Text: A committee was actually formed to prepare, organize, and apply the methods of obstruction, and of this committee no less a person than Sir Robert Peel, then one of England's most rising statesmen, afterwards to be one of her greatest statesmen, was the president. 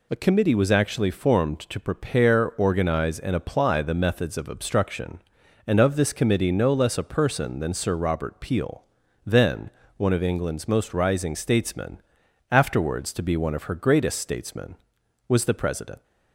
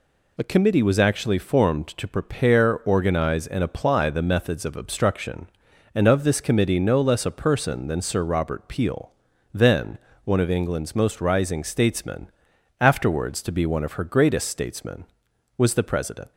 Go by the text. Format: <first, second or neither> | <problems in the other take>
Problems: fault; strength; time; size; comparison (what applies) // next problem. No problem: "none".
neither | pauses between "then" and "one"; slight; the same in both